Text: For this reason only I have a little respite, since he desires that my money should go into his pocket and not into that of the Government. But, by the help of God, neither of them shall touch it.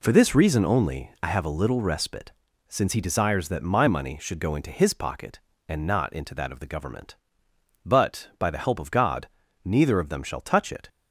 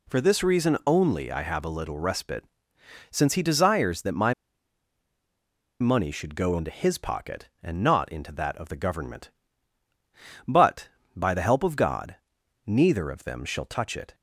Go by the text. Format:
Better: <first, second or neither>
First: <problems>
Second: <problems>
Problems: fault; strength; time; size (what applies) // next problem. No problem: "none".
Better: first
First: none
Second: pauses between "my" and "money"; strong; at 4.3 s; 1.4 s long